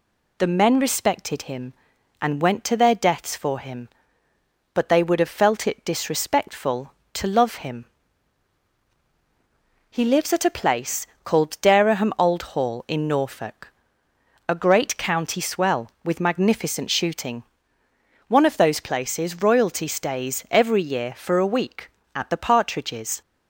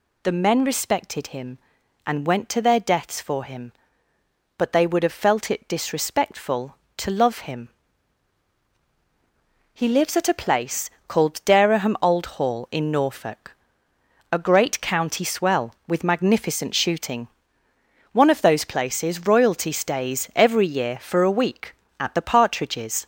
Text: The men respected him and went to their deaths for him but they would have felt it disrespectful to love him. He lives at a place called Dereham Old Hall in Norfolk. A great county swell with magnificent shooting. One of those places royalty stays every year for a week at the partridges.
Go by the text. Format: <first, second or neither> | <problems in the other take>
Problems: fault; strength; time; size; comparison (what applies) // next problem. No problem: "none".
first | gets louder; noticeable; throughout; 4 dB // pauses between "place" and "called"; slight; at 10.8 s; 0.18 s long; slight in the first